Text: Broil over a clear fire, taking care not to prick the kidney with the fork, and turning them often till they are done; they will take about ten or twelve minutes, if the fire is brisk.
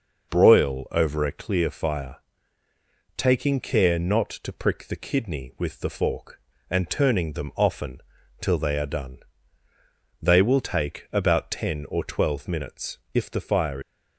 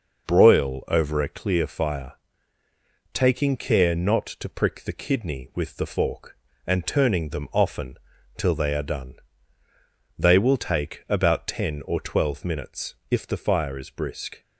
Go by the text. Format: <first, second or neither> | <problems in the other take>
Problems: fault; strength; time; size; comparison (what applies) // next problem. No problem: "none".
second | pauses between "often" and "till"; at 8.0 s; 0.38 s long; also in the second // stops before "is brisk"; at 13.8 s